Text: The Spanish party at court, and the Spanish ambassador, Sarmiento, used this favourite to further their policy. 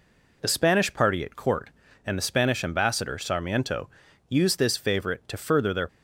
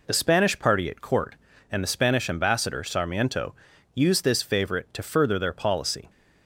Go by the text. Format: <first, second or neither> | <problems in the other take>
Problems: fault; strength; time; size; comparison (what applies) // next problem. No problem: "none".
second | stops before "policy"; at 5.8 s